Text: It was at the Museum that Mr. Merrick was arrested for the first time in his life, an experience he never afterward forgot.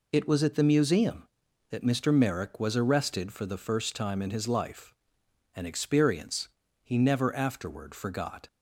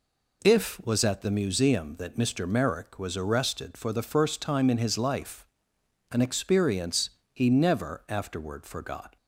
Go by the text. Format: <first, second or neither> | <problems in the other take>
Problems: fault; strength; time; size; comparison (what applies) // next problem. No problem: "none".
first | says "If" for "It"; at 0.4 s // pauses between "experience" and "he"; slight; at 7.0 s; 0.24 s long; slight in the first